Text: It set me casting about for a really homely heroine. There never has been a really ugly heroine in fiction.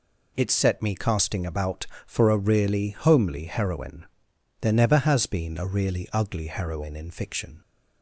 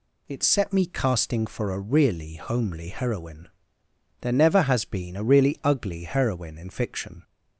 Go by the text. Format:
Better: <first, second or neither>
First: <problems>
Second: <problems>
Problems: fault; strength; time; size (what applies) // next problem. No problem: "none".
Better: first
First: none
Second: skips "about"; at 1.4 s